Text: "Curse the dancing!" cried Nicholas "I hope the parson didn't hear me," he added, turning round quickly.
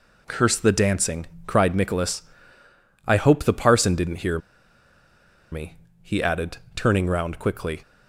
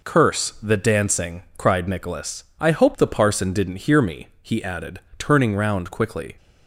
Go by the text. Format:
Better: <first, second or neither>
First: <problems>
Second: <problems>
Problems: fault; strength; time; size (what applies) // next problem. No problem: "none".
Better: second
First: pauses between "Nicholas" and "I"; noticeable; at 2.2 s; 0.84 s long // pauses between "hear" and "me"; at 4.3 s; 1.1 s long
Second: pauses between "Nicholas" and "I"; slight; at 2.4 s; 0.16 s long